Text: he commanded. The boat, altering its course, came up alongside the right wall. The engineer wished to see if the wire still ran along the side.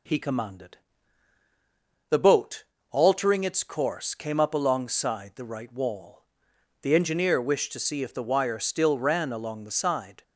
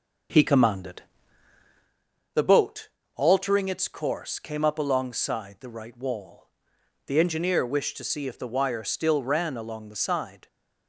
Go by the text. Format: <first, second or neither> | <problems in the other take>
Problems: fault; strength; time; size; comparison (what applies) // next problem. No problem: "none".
first | starts louder than the rest; until 1.9 s; 6.5 dB